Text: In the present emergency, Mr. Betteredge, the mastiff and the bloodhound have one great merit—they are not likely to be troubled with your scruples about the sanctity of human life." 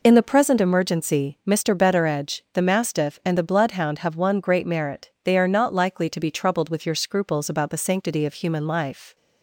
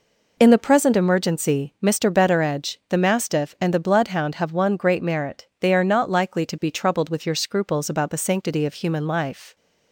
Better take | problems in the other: neither | none

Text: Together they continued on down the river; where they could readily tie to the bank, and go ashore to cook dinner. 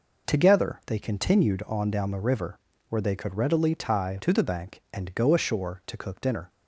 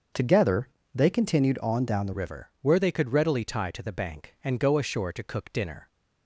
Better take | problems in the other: first | starts louder than the rest; until 1.4 s; 6 dB // pauses between "Together" and "they"; slight; at 0.6 s; 0.26 s long // changes voice at "river"; from 2.1 s on; 3.7 s long

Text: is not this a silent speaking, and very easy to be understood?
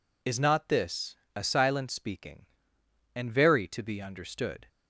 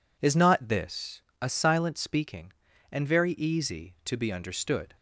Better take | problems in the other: second | pauses between "this" and "a"; slight; at 1.1 s; 0.18 s long; slight in the second // skips "easy"; at 3.6 s

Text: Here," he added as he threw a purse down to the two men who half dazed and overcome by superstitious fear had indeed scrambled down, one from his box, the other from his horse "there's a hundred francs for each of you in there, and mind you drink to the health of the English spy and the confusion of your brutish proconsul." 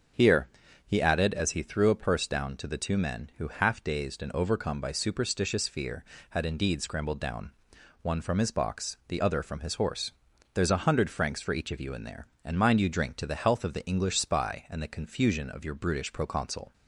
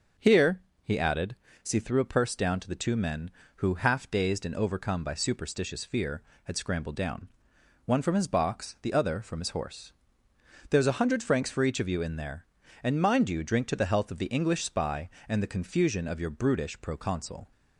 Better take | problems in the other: first | starts louder than the rest; until 1.6 s; 6 dB; also in the first // skips "indeed"; at 6.5 s // pauses between "horse" and "there's"; noticeable; at 9.9 s; 0.78 s long; also in the first

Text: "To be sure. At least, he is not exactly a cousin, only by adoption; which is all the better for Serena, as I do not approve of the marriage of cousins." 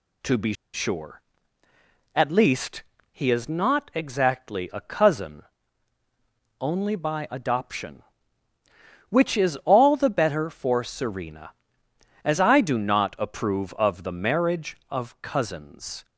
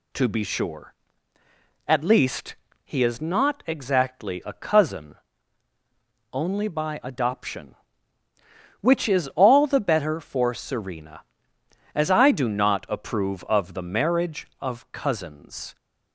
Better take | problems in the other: second | pauses between "be" and "sure"; slight; at 0.5 s; 0.20 s long

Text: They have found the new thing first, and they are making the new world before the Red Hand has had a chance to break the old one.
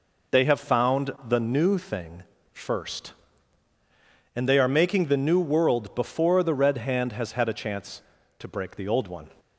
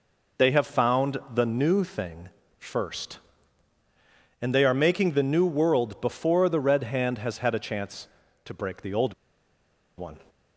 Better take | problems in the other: first | pauses between "found" and "the"; slight; at 1.1 s; 0.16 s long; slight in the first // pauses between "thing" and "first"; slight; at 2.2 s; 0.30 s long; slight in the first // pauses between "old" and "one"; noticeable; at 9.1 s; 0.84 s long

